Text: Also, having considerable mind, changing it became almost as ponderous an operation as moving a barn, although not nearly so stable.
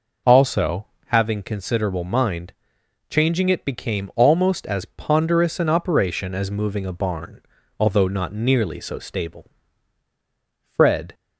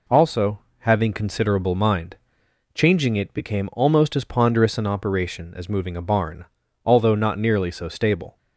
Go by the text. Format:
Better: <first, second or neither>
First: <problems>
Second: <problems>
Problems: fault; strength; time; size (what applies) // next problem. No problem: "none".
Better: second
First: goes on to say "Fred"; from 10.6 s on; 0.52 s long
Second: none